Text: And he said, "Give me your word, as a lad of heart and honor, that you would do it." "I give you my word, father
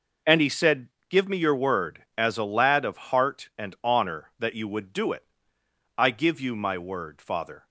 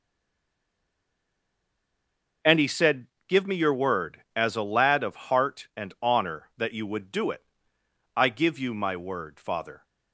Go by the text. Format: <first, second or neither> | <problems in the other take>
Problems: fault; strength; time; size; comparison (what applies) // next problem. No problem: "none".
first | stays silent before the first word; until 2.4 s; 2.4 s long